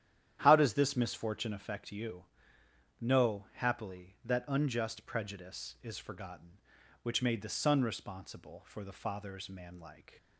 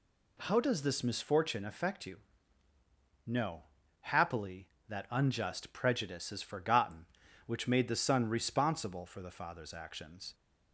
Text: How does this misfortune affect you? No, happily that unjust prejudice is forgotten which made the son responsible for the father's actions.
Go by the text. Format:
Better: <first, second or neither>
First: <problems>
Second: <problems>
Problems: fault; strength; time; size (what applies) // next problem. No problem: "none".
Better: second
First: starts louder than the rest; strong; until 1.4 s; 10.5 dB // says "manlike" for "actions"; at 9.5 s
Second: none